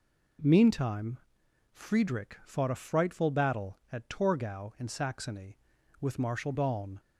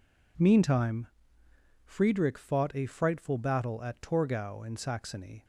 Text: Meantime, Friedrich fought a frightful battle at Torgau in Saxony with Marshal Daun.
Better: first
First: none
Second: stops before "with Marshal Daun"; at 5.4 s

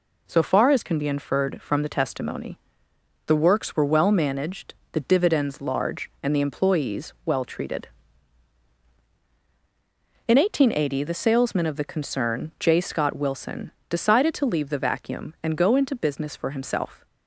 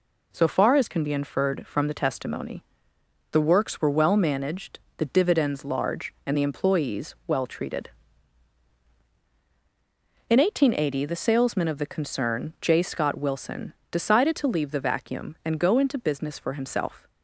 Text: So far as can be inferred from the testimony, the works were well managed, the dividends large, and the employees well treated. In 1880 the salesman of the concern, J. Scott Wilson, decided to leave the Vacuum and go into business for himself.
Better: neither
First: none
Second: none

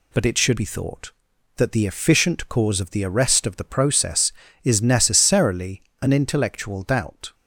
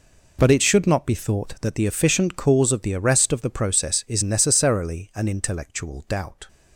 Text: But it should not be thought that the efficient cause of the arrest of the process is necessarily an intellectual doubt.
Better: second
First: skips "not"; at 0.5 s // pauses between "necessarily" and "an"; slight; at 5.8 s; 0.20 s long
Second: none

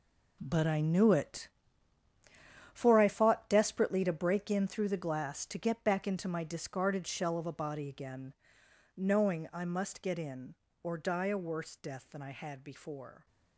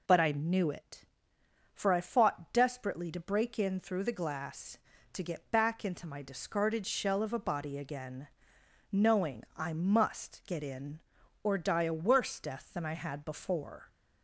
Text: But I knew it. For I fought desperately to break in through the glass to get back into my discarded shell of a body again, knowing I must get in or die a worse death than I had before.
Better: second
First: gets quieter; strong; throughout; 11.5 dB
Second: none

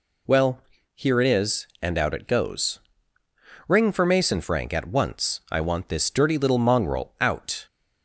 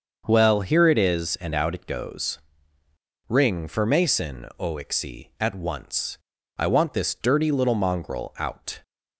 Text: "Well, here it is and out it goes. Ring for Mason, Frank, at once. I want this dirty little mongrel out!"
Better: first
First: none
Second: starts louder than the rest; until 1.2 s; 6.5 dB // says "Oixie" for "Frank"; at 4.5 s

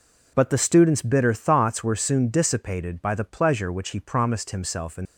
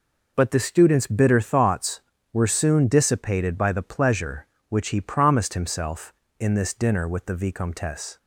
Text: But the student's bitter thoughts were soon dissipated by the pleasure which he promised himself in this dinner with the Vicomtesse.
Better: second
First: stops before "this dinner with the Vicomtesse"; at 5.0 s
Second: none

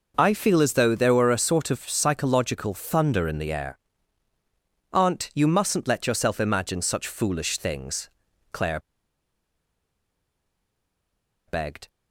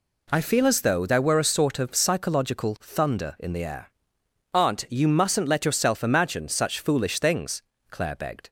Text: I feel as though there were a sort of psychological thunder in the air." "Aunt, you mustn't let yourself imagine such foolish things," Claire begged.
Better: second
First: pauses between "Claire" and "begged"; strong; at 8.7 s; 2.6 s long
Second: none

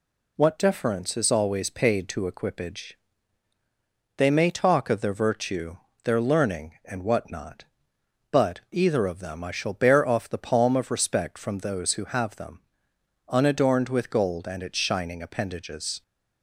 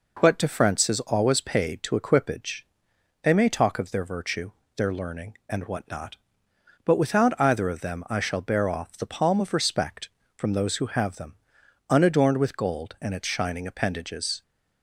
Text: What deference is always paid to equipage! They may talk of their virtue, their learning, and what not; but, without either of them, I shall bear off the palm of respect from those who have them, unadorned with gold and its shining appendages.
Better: second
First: skips "without"; at 8.6 s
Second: none

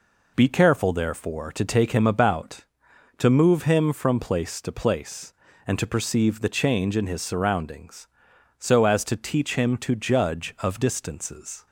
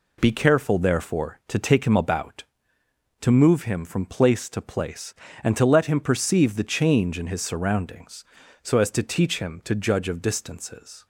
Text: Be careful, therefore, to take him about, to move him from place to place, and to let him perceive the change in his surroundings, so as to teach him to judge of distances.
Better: second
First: skips "let him"; at 5.8 s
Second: none

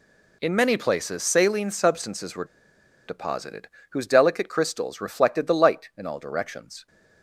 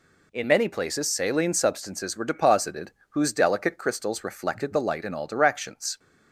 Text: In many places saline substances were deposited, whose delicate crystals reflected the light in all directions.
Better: second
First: pauses between "were" and "deposited"; noticeable; at 2.4 s; 0.63 s long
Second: none

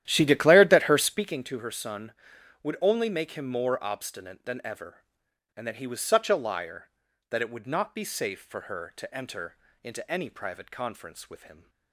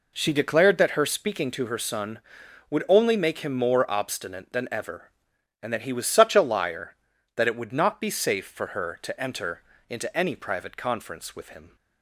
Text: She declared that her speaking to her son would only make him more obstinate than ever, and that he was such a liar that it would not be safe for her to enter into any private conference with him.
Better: second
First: starts louder than the rest; strong; until 1.4 s; 12 dB // pauses between "enter" and "into"; slight; at 9.5 s; 0.28 s long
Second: pauses between "enter" and "into"; slight; at 9.6 s; 0.28 s long

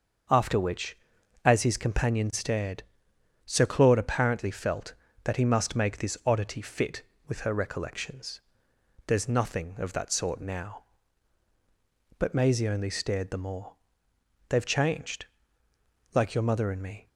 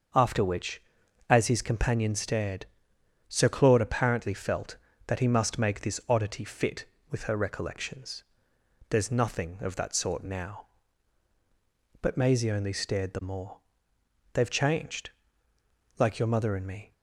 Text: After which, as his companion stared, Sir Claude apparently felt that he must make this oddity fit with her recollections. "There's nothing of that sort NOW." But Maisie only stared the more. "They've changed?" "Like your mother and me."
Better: neither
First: starts louder than the rest; until 1.7 s; 6.5 dB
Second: starts louder than the rest; until 1.6 s; 6.5 dB

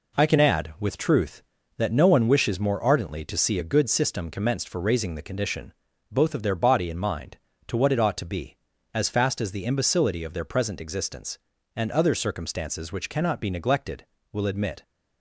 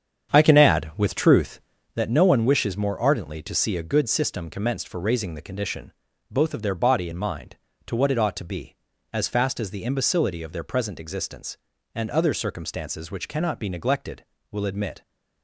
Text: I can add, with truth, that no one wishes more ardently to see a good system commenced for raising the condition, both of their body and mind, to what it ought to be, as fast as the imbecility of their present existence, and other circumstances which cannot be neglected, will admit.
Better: first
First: none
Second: starts louder than the rest; strong; until 2.0 s; 8 dB

